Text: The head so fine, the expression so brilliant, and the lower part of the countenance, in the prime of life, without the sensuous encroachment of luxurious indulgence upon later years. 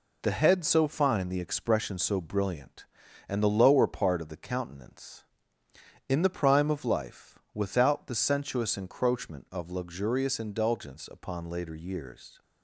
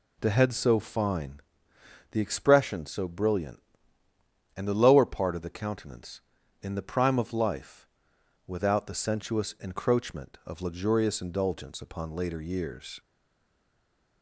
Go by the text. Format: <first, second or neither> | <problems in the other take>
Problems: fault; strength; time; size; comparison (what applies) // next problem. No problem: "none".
first | stays silent after the last word; noticeable; from 12.9 s on; 1.3 s long